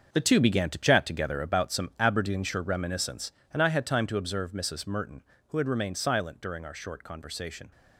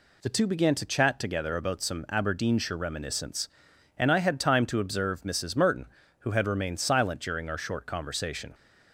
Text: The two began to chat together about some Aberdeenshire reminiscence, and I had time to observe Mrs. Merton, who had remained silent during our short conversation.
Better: second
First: gets quieter; strong; throughout; 10.5 dB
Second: none

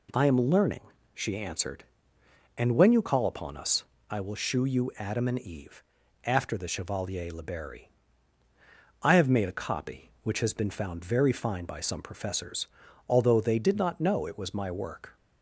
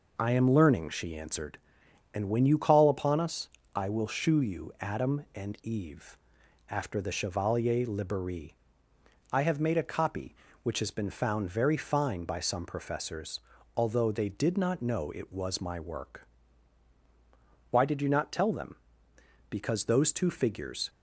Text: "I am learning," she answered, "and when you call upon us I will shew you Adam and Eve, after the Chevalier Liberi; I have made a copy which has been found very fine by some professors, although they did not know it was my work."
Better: first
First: pauses between "us" and "I"; slight; at 3.8 s; 0.26 s long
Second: pauses between "us" and "I"; slight; at 3.4 s; 0.28 s long // goes on to say "Why did you not tell them Because those two figures"; strong; from 17.6 s on; 3.2 s long

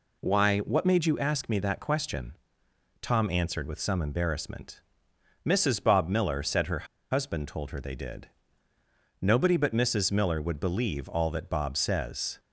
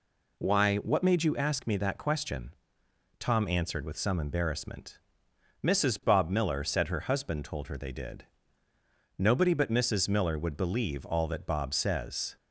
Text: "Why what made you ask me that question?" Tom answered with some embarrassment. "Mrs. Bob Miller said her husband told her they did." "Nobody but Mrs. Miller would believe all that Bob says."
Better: second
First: pauses between "her" and "husband"; slight; at 6.8 s; 0.26 s long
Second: none

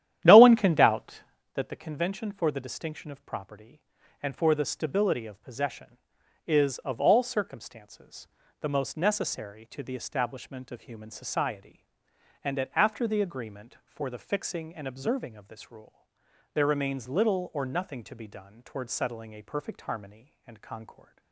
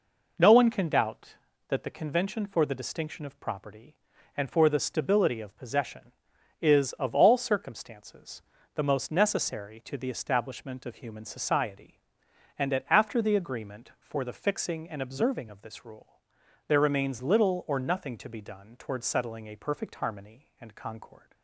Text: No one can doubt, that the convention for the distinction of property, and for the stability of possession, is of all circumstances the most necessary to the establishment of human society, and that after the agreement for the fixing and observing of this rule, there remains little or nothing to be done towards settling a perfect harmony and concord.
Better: second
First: starts louder than the rest; strong; until 1.5 s; 11 dB // pauses between "circumstances" and "the"; slight; at 8.2 s; 0.32 s long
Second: pauses between "circumstances" and "the"; slight; at 8.4 s; 0.32 s long

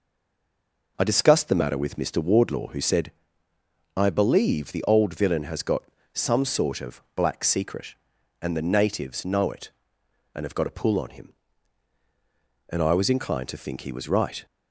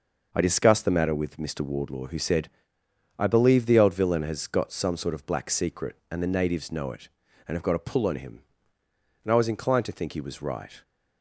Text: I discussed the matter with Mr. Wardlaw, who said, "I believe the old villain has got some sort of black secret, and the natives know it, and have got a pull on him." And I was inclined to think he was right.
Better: second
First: stays silent before the first word; slight; until 0.9 s; 0.9 s long // pauses between "got" and "some"; slight; at 5.8 s; 0.32 s long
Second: none

